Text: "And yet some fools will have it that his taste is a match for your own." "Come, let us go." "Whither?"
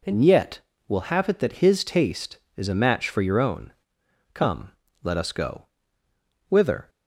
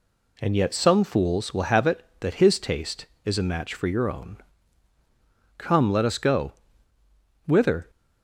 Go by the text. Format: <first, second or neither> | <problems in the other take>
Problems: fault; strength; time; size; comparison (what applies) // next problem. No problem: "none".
second | skips "some fools"; at 0.7 s